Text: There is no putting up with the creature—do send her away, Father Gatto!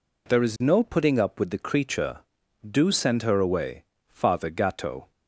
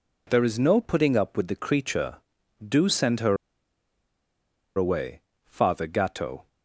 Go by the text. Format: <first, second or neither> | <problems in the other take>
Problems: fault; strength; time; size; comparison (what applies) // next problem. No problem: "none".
first | pauses between "her" and "away"; strong; at 3.3 s; 1.4 s long